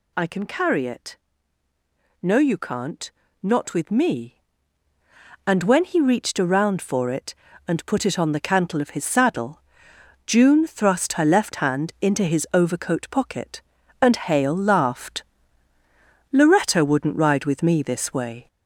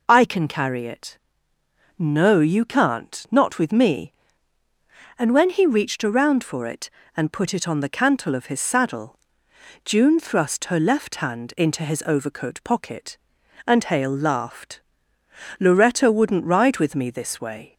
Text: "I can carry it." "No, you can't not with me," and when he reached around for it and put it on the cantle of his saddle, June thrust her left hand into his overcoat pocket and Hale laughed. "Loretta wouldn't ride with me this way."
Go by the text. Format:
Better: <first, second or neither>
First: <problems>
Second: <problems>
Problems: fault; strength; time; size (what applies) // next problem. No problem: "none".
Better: second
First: gets louder; noticeable; throughout; 5 dB // pauses between "can't" and "not"; slight; at 3.1 s; 0.30 s long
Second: none